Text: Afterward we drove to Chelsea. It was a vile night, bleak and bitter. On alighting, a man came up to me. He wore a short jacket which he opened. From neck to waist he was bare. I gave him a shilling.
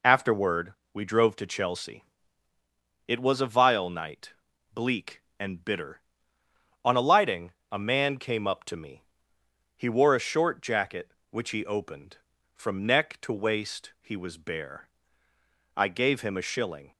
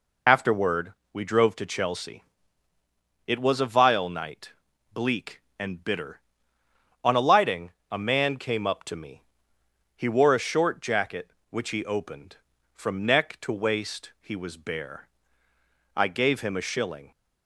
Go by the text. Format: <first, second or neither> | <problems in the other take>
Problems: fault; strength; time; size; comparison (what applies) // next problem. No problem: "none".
first | loses the start of "Afterward"; at 0.2 s; 40 ms // pauses between "Afterward" and "we"; slight; at 0.9 s; 0.20 s long; slight in the first